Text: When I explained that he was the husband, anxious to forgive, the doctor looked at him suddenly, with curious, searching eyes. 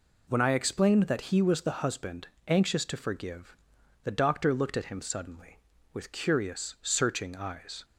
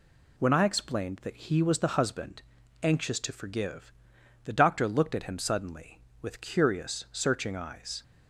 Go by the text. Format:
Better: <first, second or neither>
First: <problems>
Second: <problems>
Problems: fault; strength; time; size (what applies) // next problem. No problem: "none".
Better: neither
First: none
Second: none